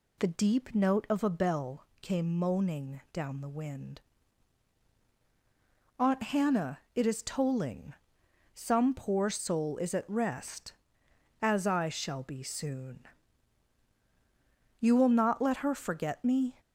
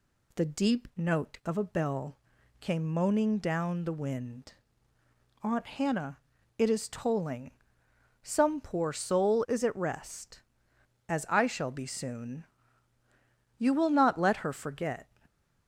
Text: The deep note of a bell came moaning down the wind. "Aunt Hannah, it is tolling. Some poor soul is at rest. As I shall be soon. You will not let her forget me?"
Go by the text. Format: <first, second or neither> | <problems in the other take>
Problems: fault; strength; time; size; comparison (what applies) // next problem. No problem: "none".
first | pauses between "bell" and "came"; noticeable; at 2.1 s; 0.46 s long; slight in the first // stops before "me"; at 15.2 s